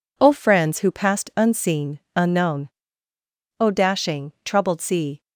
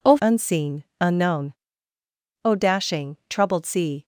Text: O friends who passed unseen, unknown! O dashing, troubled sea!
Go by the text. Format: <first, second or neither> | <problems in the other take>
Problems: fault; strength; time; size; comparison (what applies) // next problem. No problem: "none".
first | skips "friends who passed"; at 0.1 s